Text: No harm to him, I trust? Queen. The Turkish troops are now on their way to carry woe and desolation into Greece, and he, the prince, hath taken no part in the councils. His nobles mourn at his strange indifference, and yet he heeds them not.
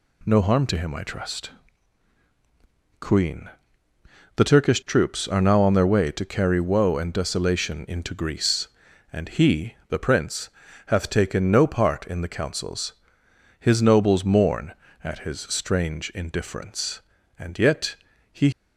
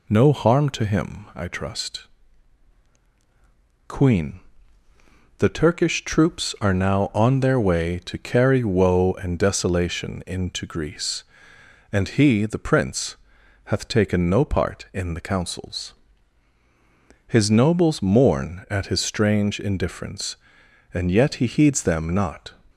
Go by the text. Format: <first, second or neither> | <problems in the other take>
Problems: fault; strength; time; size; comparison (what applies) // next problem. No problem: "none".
second | pauses between "yet" and "he"; slight; at 17.9 s; 0.36 s long // stops before "heeds them not"; at 18.5 s